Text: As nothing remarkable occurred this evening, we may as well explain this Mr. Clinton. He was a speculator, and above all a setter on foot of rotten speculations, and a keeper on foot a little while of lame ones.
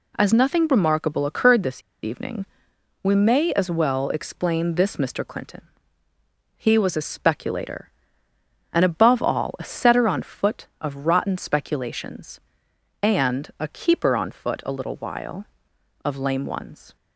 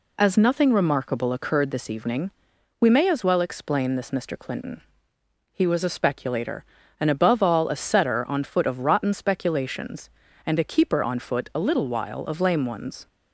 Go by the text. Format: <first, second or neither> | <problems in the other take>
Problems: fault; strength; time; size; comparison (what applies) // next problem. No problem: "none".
second | pauses between "this" and "evening"; slight; at 1.8 s; 0.21 s long